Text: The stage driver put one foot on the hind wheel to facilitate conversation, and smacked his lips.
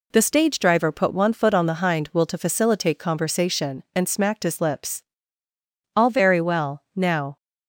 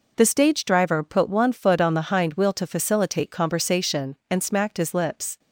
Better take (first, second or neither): second